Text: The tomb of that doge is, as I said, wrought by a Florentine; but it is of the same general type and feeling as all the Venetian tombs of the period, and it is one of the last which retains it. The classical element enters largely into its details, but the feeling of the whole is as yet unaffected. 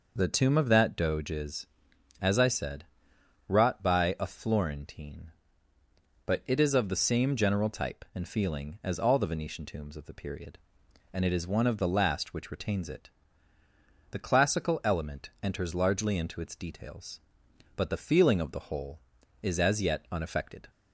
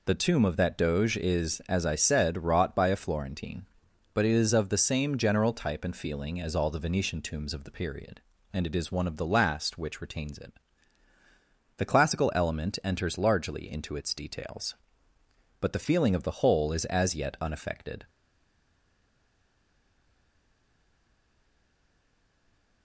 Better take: first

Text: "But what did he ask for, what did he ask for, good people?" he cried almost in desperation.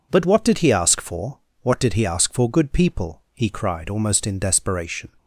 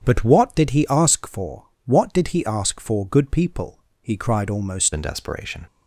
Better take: first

